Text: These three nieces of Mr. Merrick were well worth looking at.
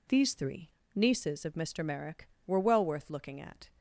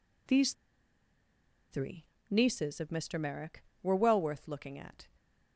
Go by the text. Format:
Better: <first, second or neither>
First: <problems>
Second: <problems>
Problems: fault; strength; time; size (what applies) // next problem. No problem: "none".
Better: first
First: pauses between "three" and "nieces"; slight; at 0.6 s; 0.26 s long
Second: pauses between "These" and "three"; at 0.5 s; 1.1 s long // pauses between "three" and "nieces"; slight; at 2.0 s; 0.26 s long